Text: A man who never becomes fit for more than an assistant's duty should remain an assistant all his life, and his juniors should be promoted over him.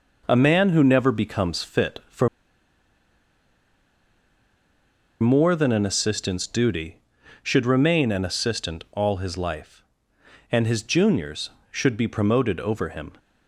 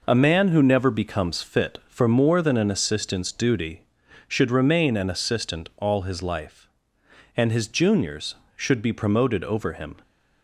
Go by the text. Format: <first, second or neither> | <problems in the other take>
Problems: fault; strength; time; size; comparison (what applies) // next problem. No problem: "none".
second | pauses between "for" and "more"; strong; at 2.2 s; 2.9 s long